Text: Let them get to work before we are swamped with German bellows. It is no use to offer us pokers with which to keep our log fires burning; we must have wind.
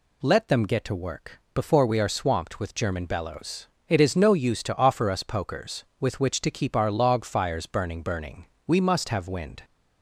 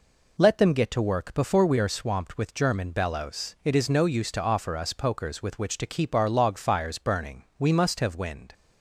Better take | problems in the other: second | pauses between "work" and "before"; slight; at 1.3 s; 0.16 s long // says "burning" twice; at 8.0 s

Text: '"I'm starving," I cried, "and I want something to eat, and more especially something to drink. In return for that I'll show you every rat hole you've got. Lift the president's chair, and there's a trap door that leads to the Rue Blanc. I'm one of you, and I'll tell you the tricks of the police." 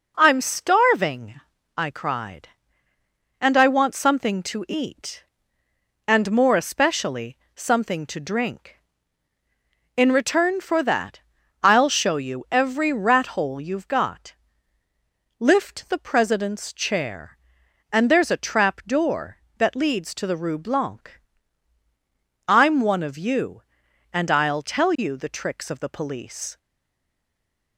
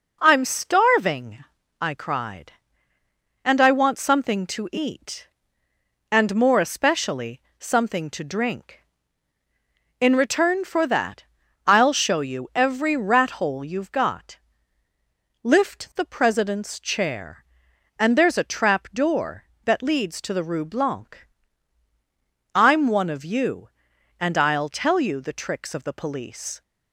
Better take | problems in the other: second | pauses between "especially" and "something"; slight; at 7.3 s; 0.20 s long; slight in the second // pauses between "that" and "I'll"; noticeable; at 11.1 s; 0.46 s long; noticeable in the second // stays silent after the last word; noticeable; from 26.5 s on; 1.2 s long

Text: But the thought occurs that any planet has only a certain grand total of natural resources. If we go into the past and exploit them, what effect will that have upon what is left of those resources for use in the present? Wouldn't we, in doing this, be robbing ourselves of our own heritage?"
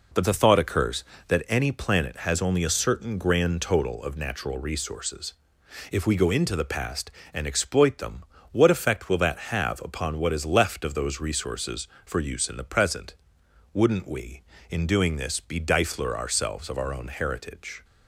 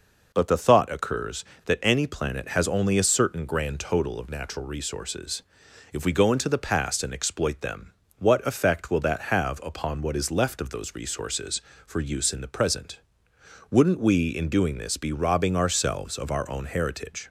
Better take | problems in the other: second | says "difler" for "robbing"; at 15.6 s

